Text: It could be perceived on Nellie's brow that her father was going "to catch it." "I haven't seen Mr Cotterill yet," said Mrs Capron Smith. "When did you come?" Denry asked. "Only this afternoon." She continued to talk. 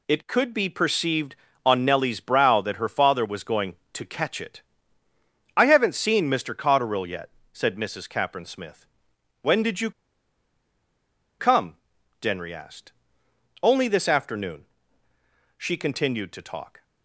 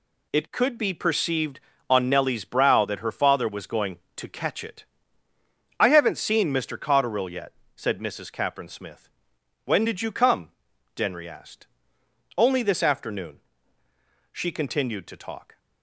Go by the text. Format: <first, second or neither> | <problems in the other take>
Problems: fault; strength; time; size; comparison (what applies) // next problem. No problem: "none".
second | pauses between "you" and "come"; strong; at 9.9 s; 1.4 s long